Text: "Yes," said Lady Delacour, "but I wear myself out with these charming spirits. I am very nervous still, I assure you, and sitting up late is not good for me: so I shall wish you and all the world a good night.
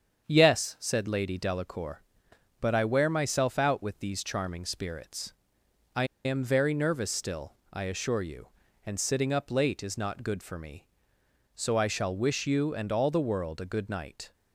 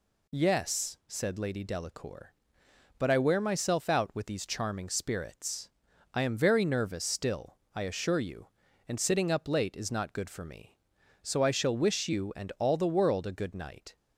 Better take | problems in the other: second | starts louder than the rest; strong; until 1.3 s; 7.5 dB // pauses between "I" and "am"; slight; at 6.0 s; 0.20 s long

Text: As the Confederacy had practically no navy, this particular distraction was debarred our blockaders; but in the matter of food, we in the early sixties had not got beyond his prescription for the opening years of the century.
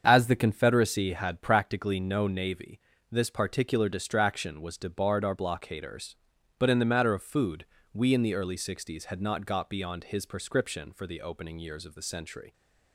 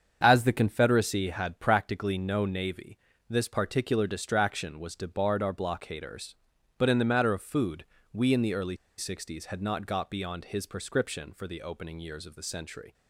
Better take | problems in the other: first | starts louder than the rest; until 1.2 s; 7 dB; also in the first // pauses between "early" and "sixties"; slight; at 8.7 s; 0.21 s long

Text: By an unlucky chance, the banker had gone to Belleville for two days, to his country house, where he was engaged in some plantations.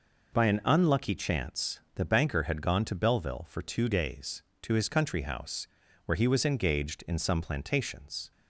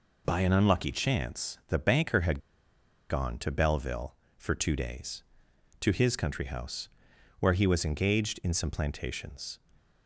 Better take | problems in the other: first | pauses between "had" and "gone"; noticeable; at 2.3 s; 0.70 s long

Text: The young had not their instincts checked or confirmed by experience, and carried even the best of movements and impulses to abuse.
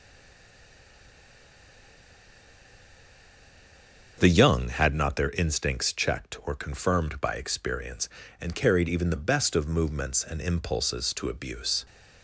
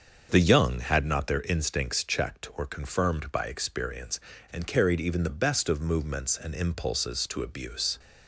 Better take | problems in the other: second | stays silent before the first word; strong; until 4.1 s; 4.1 s long // starts louder than the rest; until 5.1 s; 6.5 dB; also in the second

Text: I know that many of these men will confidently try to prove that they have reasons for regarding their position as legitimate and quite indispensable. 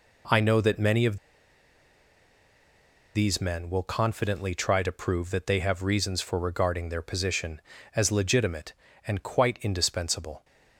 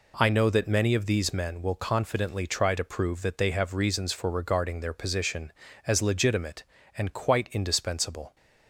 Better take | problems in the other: second | pauses between "of" and "these"; strong; at 1.1 s; 1.9 s long

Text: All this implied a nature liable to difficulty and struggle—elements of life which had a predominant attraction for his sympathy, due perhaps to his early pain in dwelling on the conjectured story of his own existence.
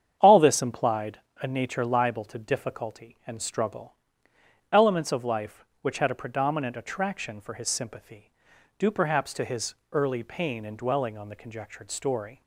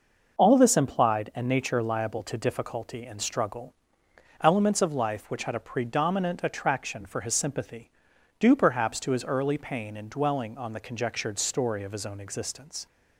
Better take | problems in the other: second | starts louder than the rest; strong; until 1.2 s; 8.5 dB // pauses between "implied" and "a"; slight; at 1.2 s; 0.20 s long // pauses between "his" and "early"; slight; at 9.7 s; 0.18 s long // stops before "of his own existence"; at 12.4 s

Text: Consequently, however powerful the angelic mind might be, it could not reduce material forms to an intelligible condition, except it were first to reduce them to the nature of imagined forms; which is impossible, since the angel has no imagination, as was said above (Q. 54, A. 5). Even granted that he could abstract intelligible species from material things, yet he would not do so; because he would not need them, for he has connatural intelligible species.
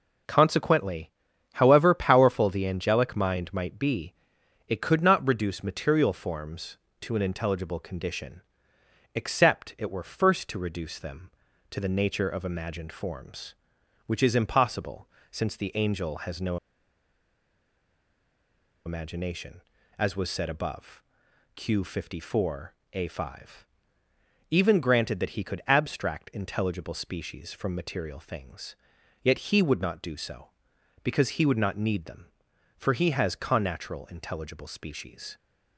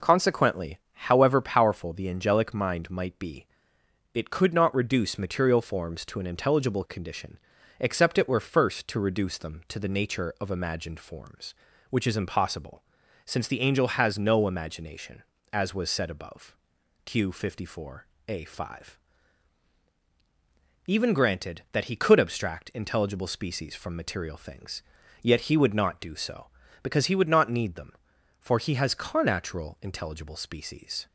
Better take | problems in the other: second | pauses between "no" and "imagination"; strong; at 16.5 s; 2.2 s long

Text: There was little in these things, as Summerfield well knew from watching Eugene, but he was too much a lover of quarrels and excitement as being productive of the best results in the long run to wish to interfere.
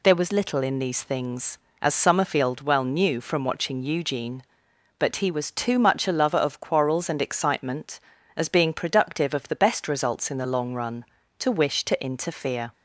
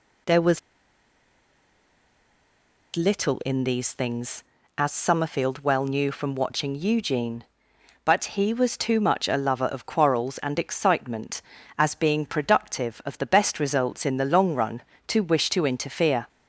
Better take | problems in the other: first | pauses between "was" and "little"; strong; at 0.5 s; 2.3 s long

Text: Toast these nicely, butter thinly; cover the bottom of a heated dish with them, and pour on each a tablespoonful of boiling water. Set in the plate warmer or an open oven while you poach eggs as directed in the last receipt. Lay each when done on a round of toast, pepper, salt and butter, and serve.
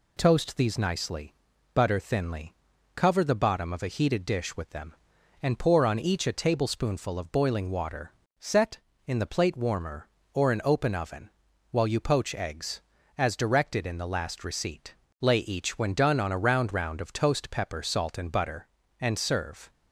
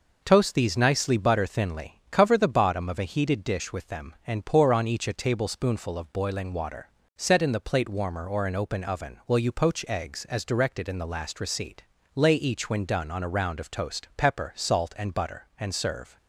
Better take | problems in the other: second | pauses between "oven" and "while"; at 11.2 s; 0.40 s long // says "round" twice; at 16.7 s

